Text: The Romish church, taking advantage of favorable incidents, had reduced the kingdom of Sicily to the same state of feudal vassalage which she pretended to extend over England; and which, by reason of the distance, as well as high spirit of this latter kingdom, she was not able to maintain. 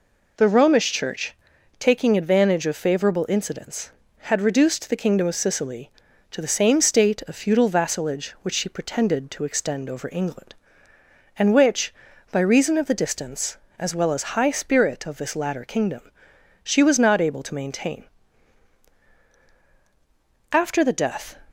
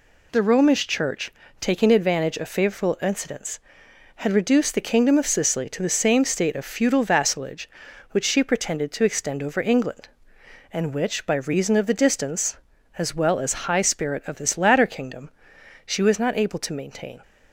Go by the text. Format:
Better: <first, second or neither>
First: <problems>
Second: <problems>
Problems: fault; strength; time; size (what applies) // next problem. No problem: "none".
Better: second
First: goes on to say "After the death"; noticeable; from 20.5 s on; 0.86 s long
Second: none